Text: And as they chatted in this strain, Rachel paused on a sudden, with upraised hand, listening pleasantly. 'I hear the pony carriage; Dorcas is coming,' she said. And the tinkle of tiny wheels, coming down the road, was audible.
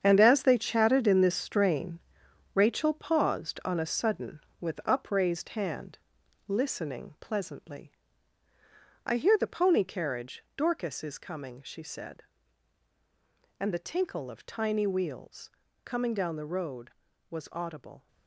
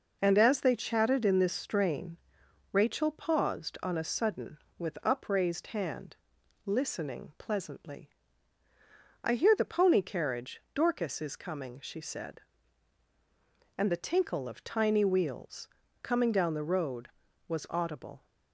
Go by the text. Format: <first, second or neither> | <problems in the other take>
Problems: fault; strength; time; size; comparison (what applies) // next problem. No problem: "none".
second | gets quieter; strong; throughout; 10.5 dB